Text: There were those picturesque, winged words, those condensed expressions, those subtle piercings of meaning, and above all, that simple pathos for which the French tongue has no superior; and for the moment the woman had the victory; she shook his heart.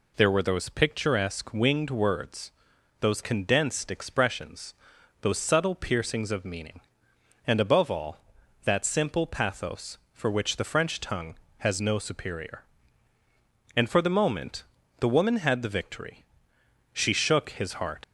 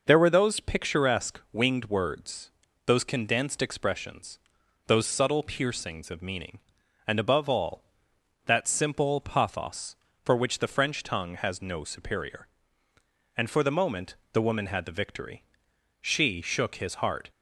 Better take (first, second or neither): second